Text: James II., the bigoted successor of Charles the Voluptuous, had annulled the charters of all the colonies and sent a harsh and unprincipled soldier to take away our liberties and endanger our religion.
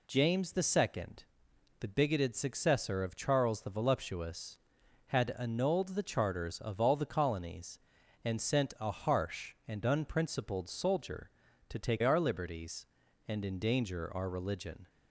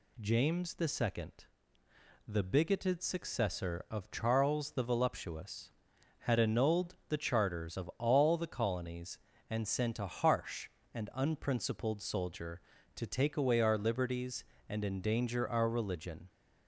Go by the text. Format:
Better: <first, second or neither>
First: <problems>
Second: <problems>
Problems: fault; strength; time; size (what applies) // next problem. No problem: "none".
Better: second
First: skips "away"; at 12.0 s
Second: none